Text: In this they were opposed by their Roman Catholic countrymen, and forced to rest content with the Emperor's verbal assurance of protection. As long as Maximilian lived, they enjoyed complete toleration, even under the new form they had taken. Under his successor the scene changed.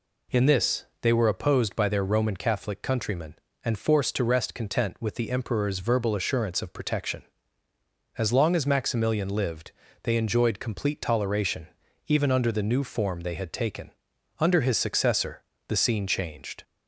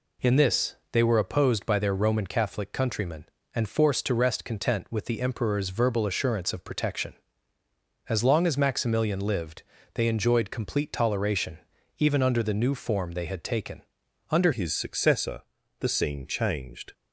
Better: first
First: pauses between "this" and "they"; slight; at 0.8 s; 0.16 s long // pauses between "successor" and "the"; slight; at 15.4 s; 0.26 s long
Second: pauses between "this" and "they"; slight; at 0.7 s; 0.16 s long // changes voice at "his"; from 14.5 s on; 2.4 s long // pauses between "successor" and "the"; slight; at 15.4 s; 0.36 s long

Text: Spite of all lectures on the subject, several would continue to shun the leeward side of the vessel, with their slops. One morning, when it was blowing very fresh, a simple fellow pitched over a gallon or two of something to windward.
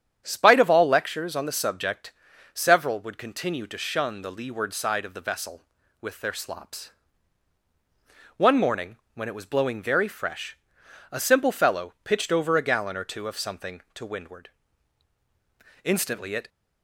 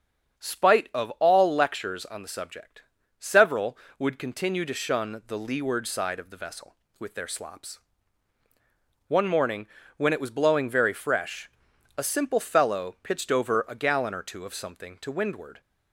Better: second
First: starts louder than the rest; strong; until 1.2 s; 9 dB // goes on to say "Instantly it"; noticeable; from 15.8 s on; 0.64 s long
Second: starts louder than the rest; strong; until 1.5 s; 7.5 dB

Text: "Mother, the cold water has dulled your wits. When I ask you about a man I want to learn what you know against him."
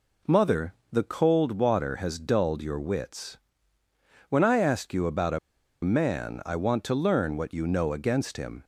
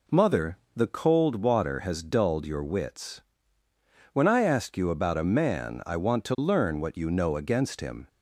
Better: second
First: pauses between "a" and "man"; at 5.3 s; 0.45 s long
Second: none

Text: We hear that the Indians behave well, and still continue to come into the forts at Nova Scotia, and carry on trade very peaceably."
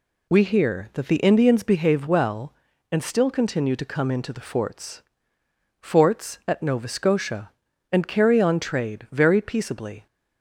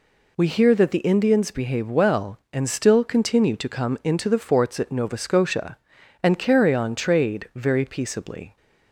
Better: second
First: says "forts" twice; at 5.8 s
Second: none

